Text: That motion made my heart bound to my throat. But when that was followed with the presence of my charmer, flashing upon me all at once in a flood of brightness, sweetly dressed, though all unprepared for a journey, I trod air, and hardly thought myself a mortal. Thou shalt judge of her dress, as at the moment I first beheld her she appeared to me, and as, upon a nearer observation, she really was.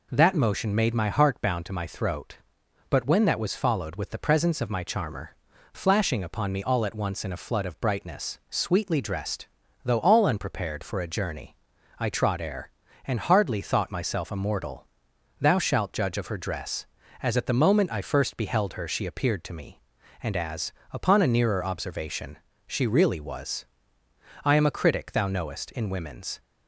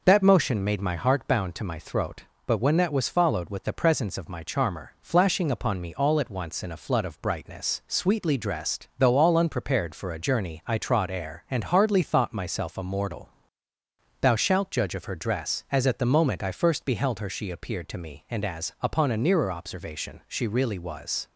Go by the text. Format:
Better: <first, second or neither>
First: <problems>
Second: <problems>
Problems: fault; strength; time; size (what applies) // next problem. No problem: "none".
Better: second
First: goes on to say "I am a critic thou knowest in women's"; strong; from 24.4 s on; 1.9 s long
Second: none